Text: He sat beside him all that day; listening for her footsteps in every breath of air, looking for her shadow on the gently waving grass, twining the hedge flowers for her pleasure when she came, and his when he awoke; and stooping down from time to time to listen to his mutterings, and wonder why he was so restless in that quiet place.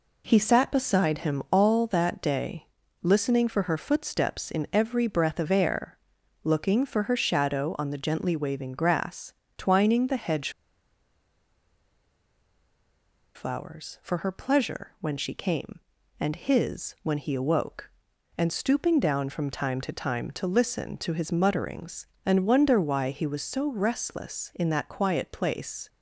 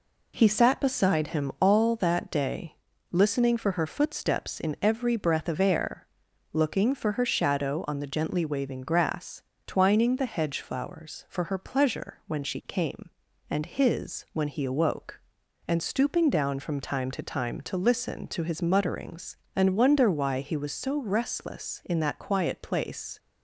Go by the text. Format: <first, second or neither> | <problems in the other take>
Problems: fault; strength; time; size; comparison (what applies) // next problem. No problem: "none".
second | pauses between "hedge" and "flowers"; strong; at 10.4 s; 2.8 s long